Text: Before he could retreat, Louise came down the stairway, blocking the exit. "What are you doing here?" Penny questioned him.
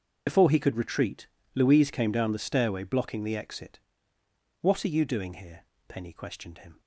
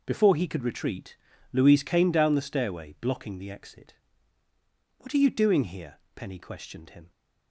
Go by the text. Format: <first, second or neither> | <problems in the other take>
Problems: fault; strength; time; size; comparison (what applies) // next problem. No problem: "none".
second | loses the start of "Before"; at 0.2 s; 45 ms // starts louder than the rest; until 1.2 s; 6.5 dB